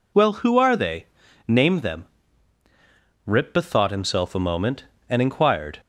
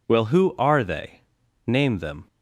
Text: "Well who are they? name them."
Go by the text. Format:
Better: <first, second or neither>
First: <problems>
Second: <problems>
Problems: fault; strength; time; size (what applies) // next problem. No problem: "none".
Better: second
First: goes on to say "Rip bethought himself a moment and inquired"; strong; from 3.2 s on; 2.5 s long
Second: none